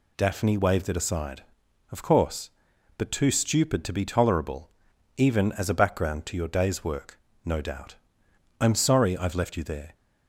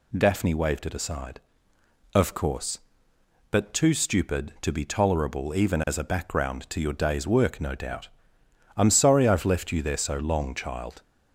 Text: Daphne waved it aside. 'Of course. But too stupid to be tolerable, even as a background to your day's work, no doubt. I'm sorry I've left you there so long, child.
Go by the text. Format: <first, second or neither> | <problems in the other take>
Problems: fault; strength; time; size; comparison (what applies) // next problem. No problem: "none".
second | stops before "so long child"; at 9.9 s